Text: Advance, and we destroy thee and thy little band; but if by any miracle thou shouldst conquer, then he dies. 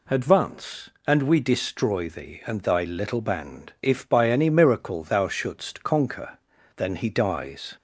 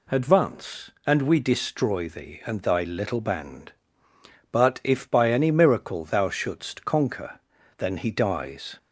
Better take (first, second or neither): second